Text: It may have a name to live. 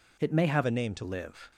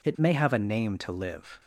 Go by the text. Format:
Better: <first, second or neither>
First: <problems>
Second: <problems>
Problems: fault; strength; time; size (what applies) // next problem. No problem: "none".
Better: second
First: changes voice from "a" to "to"; from 0.6 to 1.0 s; 0.4 s long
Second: none